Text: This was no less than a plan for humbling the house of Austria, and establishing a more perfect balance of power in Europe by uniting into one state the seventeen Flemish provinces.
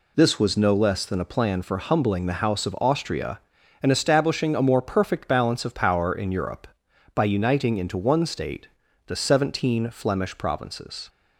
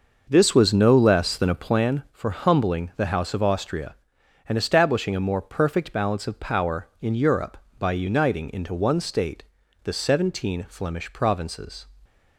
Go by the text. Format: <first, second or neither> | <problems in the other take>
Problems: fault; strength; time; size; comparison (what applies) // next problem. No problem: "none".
first | starts louder than the rest; noticeable; until 1.9 s; 6 dB // pauses between "state" and "the"; at 9.4 s; 0.40 s long; also in the first